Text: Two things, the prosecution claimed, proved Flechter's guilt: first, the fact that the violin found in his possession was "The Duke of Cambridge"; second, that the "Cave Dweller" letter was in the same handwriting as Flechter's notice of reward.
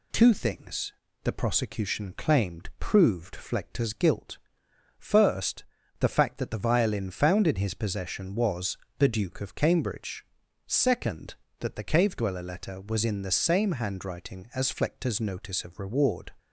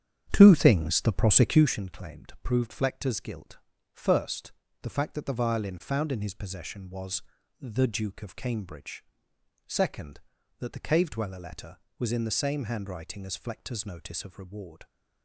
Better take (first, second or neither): first